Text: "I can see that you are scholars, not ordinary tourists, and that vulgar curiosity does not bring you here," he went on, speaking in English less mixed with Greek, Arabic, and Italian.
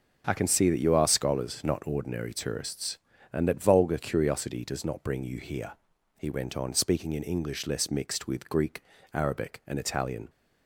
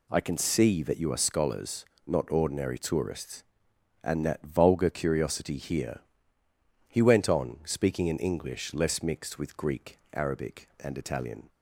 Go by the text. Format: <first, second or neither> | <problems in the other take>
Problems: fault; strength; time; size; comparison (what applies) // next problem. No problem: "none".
first | skips "does not bring you"; at 5.5 s